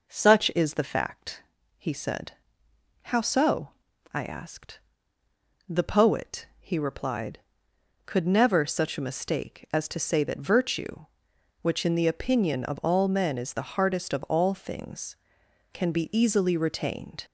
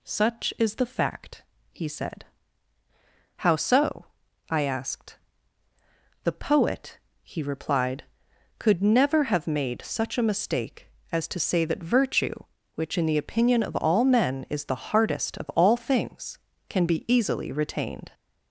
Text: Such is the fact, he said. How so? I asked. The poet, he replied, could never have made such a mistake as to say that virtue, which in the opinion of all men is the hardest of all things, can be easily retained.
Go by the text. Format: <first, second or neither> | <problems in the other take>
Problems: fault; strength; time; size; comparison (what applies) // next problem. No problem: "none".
second | skips "have made"; at 8.6 s